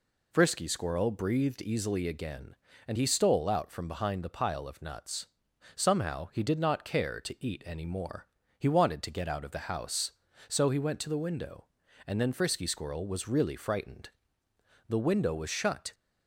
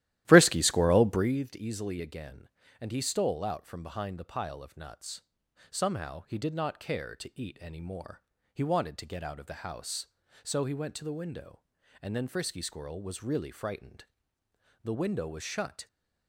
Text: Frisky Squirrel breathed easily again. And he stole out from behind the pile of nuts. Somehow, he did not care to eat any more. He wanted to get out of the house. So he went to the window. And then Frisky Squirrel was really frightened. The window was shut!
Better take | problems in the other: first | starts louder than the rest; strong; until 1.4 s; 14 dB

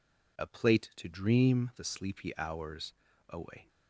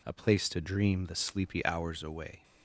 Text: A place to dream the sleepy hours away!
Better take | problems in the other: second | says "plate" for "place"; at 0.4 s // pauses between "hours" and "away"; at 2.9 s; 0.38 s long

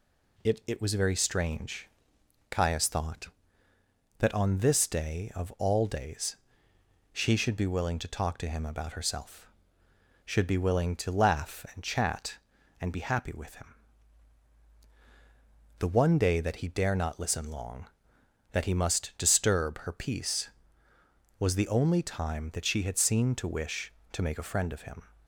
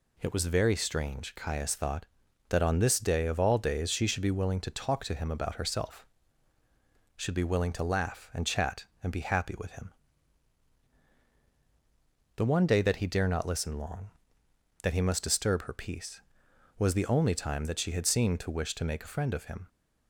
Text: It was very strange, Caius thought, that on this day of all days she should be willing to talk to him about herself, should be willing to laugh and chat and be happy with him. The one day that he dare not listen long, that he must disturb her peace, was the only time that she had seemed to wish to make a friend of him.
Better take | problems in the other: second | says "It" twice; at 0.6 s // pauses between "days" and "she"; noticeable; at 6.3 s; 0.76 s long

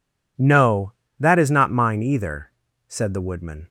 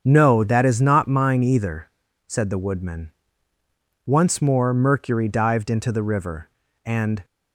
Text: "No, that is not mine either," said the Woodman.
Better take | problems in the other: first | starts louder than the rest; strong; until 1.0 s; 7 dB // goes on to say "Once more Mercury dived into the river and"; strong; from 4.0 s on; 3.1 s long

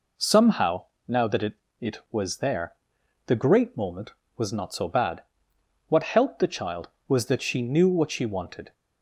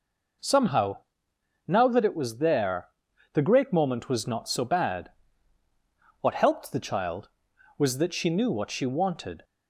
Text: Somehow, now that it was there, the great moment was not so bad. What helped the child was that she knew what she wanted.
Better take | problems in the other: second | says "it" twice; at 1.7 s

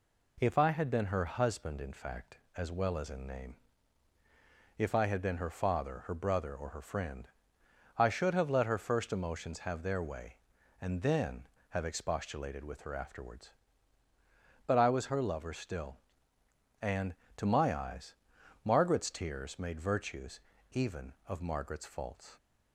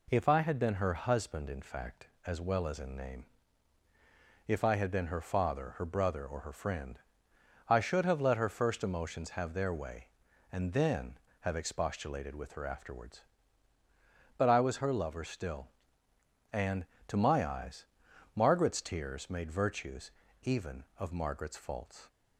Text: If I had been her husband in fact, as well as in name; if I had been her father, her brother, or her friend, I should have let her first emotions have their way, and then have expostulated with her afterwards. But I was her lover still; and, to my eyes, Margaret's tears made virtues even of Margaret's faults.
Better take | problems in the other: neither | pauses between "virtues" and "even"; slight; the same in both

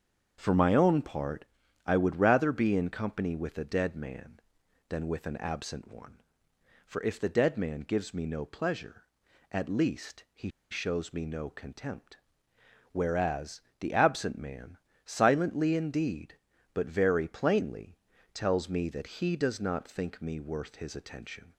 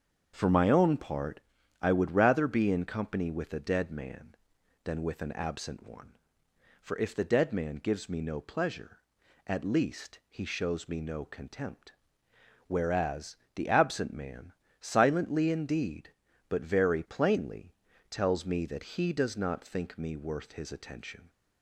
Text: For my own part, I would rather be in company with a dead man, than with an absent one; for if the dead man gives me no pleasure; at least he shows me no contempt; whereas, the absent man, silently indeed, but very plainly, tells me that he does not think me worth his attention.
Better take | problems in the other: second | starts louder than the rest; strong; until 1.4 s; 7 dB; strong in the second // pauses between "he" and "shows"; slight; at 10.4 s; 0.21 s long

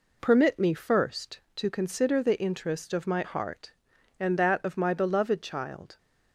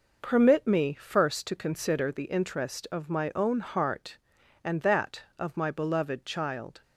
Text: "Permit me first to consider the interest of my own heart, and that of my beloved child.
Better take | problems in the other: second | skips "own"; at 3.2 s

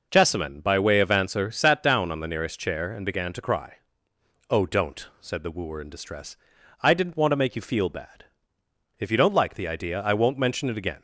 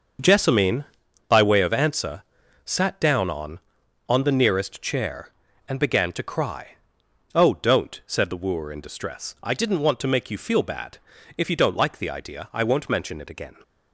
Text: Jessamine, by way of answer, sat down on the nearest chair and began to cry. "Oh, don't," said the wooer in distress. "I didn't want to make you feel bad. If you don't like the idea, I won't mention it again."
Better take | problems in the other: first | starts louder than the rest; until 1.6 s; 6.5 dB // says "on" twice; at 4.0 s

